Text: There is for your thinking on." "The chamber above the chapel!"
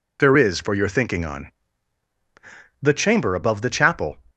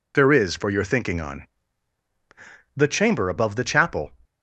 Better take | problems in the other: neither | none

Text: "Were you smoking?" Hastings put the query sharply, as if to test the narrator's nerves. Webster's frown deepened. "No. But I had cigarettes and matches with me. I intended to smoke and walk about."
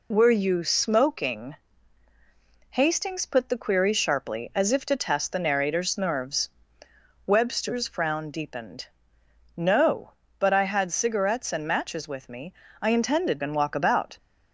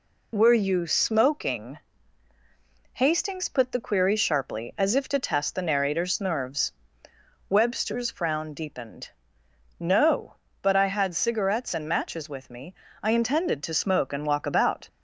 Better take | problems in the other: second | skips "to smoke"; at 13.4 s

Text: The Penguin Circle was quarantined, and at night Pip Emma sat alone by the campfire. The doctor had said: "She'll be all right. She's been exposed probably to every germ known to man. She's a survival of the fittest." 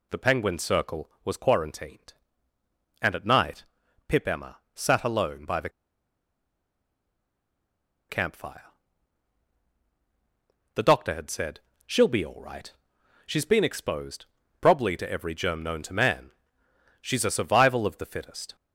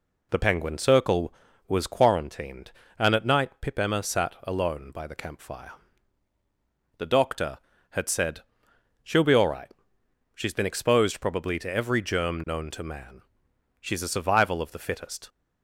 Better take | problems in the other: second | pauses between "night" and "Pip"; at 3.6 s; 0.44 s long // pauses between "Emma" and "sat"; slight; at 4.5 s; 0.16 s long // pauses between "the" and "campfire"; strong; at 5.6 s; 2.4 s long // pauses between "exposed" and "probably"; slight; at 14.2 s; 0.34 s long

